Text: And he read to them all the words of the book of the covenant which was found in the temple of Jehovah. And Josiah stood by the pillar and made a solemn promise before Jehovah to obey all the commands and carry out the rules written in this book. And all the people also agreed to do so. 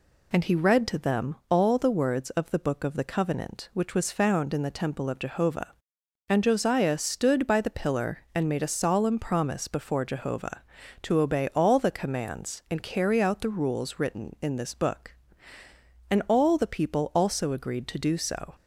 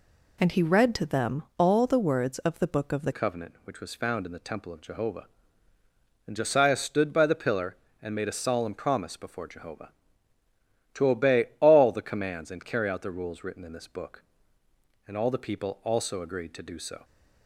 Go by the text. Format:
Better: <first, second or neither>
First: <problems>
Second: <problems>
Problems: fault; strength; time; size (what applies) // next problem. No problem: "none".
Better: first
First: none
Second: changes voice at "covenant"; from 3.1 s on; 13.9 s long